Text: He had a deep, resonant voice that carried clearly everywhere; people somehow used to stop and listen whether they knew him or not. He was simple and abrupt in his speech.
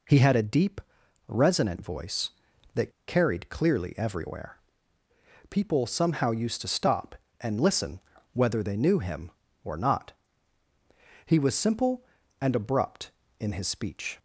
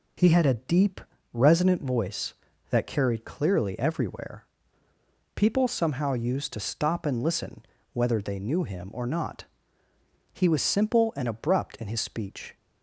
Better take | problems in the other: second | pauses between "that" and "carried"; slight; at 2.8 s; 0.17 s long // pauses between "listen" and "whether"; slight; at 8.0 s; 0.32 s long; slight in the second

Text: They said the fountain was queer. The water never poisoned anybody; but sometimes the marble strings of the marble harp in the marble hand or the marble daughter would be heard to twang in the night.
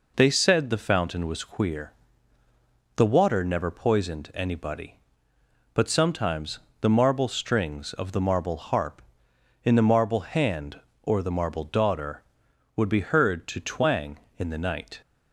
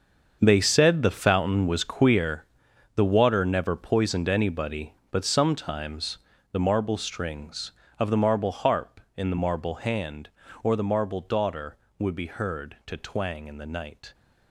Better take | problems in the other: first | gets quieter; strong; throughout; 13.5 dB // pauses between "sometimes" and "the"; slight; at 6.1 s; 0.36 s long; slight in the first

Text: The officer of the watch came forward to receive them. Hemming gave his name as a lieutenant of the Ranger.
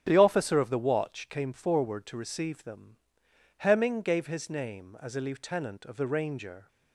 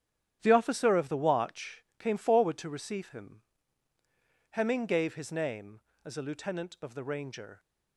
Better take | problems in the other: first | starts louder than the rest; strong; until 1.4 s; 10 dB; strong in the first // says "him" for "them"; at 3.0 s

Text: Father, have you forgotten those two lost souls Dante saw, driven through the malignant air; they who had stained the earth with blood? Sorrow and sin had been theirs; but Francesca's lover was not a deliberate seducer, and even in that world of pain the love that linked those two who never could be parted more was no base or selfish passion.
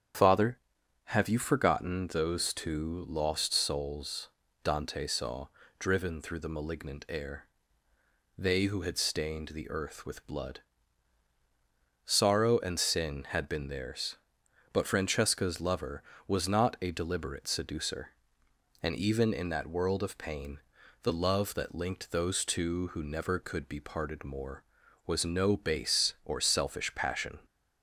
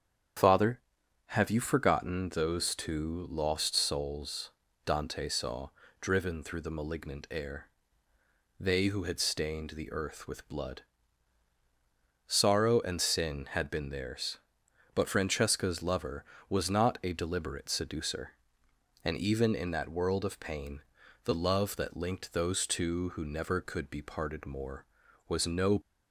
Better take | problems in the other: first | starts louder than the rest; strong; until 1.8 s; 8.5 dB; strong in the first // pauses between "souls" and "Dante"; slight; at 4.5 s; 0.34 s long; slight in the first // pauses between "pain" and "the"; at 20.8 s; 0.42 s long; also in the first // stops before "base or selfish passion"; at 25.8 s

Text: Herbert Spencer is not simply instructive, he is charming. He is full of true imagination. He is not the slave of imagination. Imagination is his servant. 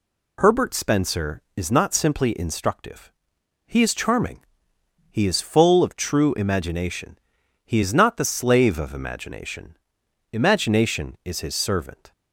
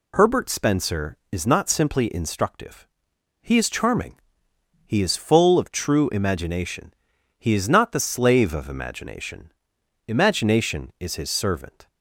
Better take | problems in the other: neither | none

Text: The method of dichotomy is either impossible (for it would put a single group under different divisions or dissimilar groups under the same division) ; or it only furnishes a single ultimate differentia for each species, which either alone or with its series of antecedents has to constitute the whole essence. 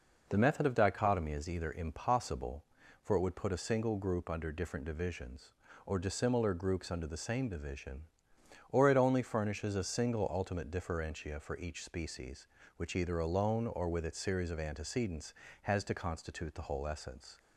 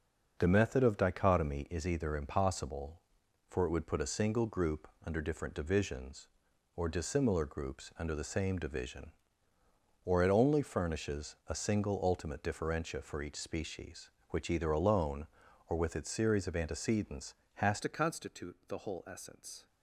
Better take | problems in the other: first | pauses between "group" and "under"; slight; at 4.8 s; 0.16 s long // changes voice at "to"; from 17.8 s on; 1.8 s long

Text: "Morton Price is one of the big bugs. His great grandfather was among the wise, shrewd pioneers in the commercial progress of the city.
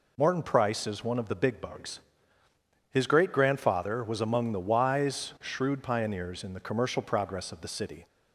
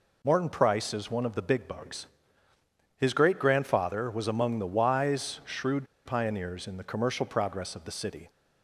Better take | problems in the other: first | pauses between "shrewd" and "pioneers"; slight; at 5.8 s; 0.19 s long

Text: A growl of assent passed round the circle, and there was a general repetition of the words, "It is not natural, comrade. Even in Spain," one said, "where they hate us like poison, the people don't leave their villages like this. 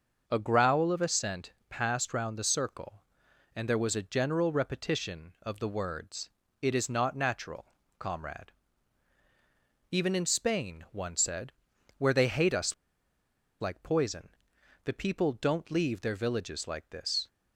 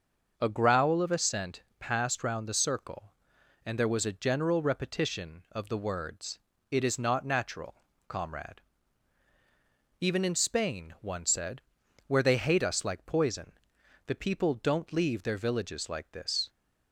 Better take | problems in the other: second | starts louder than the rest; until 1.2 s; 6.5 dB; also in the second // pauses between "assent" and "passed"; slight; at 1.5 s; 0.18 s long; slight in the second // pauses between "us" and "like"; noticeable; at 12.7 s; 0.86 s long

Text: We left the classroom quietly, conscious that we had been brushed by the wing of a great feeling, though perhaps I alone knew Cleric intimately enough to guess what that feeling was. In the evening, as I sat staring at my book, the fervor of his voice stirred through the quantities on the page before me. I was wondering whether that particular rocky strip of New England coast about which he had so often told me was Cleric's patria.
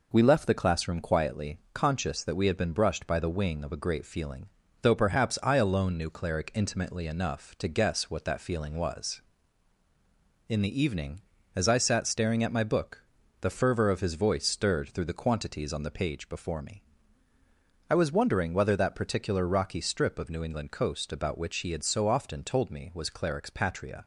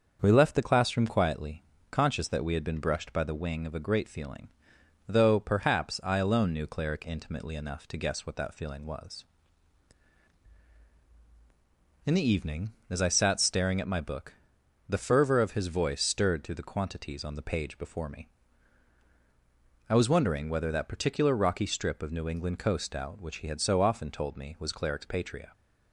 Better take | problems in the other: first | starts louder than the rest; until 1.2 s; 6.5 dB // says "out" for "about"; at 22.9 s

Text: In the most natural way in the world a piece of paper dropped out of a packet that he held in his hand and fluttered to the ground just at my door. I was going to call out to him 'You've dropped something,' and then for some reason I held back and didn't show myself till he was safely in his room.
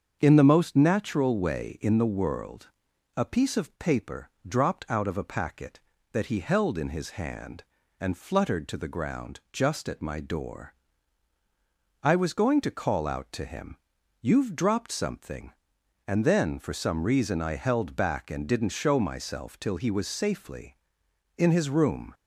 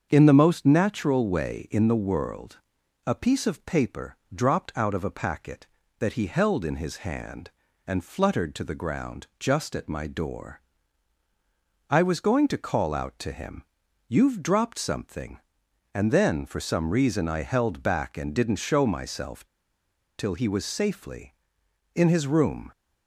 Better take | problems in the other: first | starts louder than the rest; until 1.1 s; 7 dB; also in the first // pauses between "world" and "a"; noticeable; at 2.5 s; 0.48 s long; noticeable in the first // pauses between "paper" and "dropped"; slight; at 4.1 s; 0.18 s long; slight in the first // pauses between "him" and "You've"; at 13.6 s; 0.42 s long; also in the first // pauses between "myself" and "till"; noticeable; at 19.4 s; 0.73 s long

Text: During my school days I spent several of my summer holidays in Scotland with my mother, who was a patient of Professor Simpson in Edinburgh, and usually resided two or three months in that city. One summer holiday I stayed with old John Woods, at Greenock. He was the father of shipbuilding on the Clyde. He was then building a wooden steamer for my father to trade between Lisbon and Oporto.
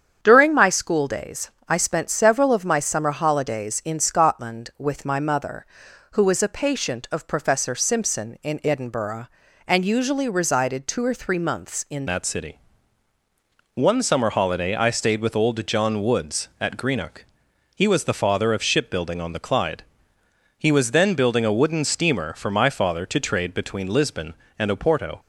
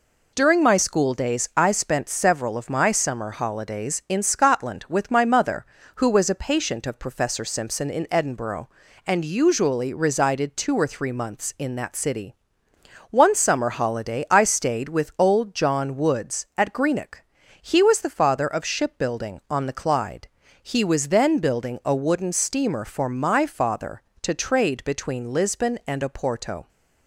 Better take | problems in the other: second | starts louder than the rest; strong; until 1.2 s; 8 dB // pauses between "days" and "I"; slight; at 1.4 s; 0.20 s long // changes voice at "that"; from 12.0 s on; 13.1 s long

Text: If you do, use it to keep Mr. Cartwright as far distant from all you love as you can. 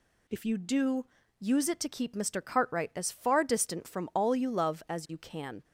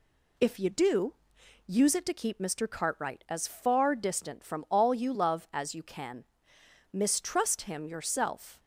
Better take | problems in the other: first | goes on to say "Mistrust him yourself"; from 6.9 s on; 1.6 s long

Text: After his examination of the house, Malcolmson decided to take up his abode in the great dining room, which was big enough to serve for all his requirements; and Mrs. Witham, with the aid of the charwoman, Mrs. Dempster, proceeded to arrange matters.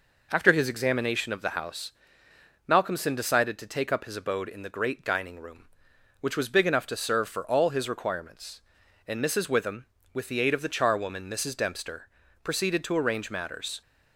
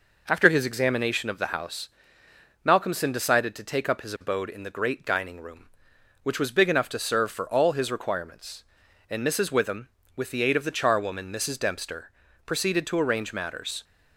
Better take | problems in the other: neither | none

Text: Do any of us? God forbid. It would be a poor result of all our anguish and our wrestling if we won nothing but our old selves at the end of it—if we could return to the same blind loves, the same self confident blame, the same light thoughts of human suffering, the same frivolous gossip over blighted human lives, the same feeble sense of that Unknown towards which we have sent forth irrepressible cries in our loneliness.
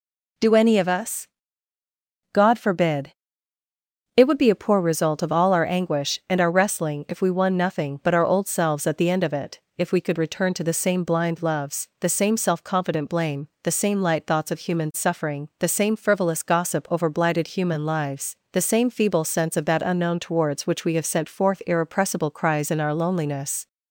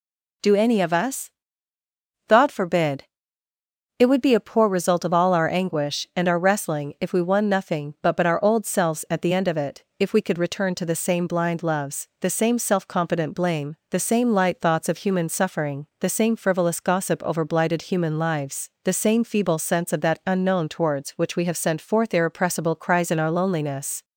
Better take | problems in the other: first | says "but" twice; at 8.1 s

